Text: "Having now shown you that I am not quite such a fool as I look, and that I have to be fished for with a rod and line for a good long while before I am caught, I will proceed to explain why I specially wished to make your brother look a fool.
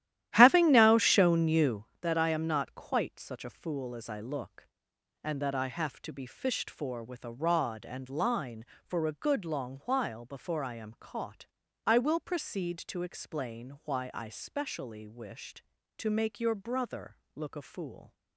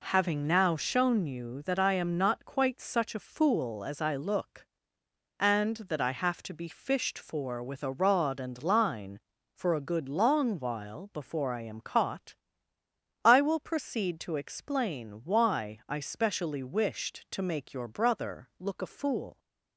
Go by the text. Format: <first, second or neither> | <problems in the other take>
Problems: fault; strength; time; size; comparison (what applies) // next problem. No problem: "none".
second | starts louder than the rest; strong; until 1.9 s; 13 dB // pauses between "brother" and "look"; slight; at 17.1 s; 0.18 s long